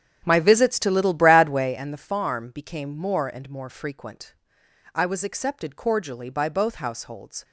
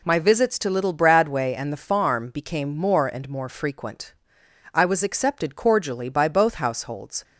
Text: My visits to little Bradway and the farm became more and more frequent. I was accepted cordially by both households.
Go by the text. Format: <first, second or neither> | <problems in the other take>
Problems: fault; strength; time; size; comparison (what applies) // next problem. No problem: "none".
second | starts louder than the rest; strong; until 1.9 s; 9 dB